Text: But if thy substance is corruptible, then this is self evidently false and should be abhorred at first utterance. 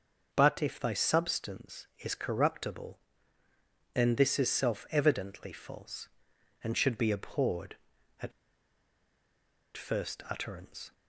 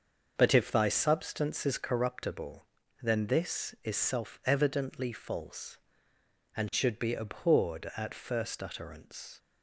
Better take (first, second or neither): second